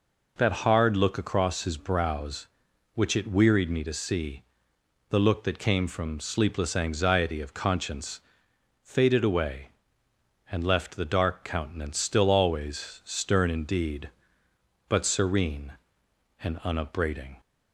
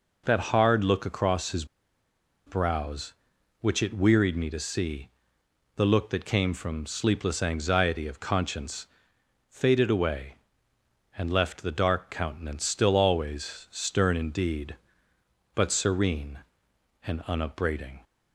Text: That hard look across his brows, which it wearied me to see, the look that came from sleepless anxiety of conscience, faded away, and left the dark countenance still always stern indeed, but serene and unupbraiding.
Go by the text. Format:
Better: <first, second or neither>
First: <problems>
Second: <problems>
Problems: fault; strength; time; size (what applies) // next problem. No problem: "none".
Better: first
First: none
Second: pauses between "his" and "brows"; noticeable; at 1.6 s; 0.81 s long